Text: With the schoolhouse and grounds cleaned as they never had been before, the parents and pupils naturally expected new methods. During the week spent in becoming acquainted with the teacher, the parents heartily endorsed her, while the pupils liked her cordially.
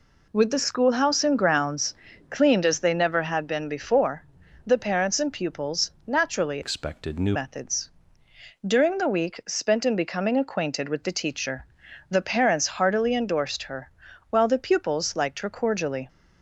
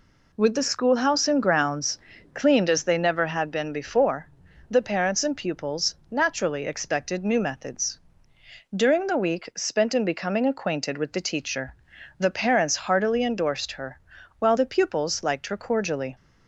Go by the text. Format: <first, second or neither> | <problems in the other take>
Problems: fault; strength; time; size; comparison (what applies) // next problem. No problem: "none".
second | pauses between "grounds" and "cleaned"; slight; at 1.9 s; 0.34 s long; slight in the second // pauses between "pupils" and "naturally"; slight; at 5.8 s; 0.16 s long; slight in the second // changes voice from "expected" to "new"; from 6.6 to 7.3 s; 0.7 s long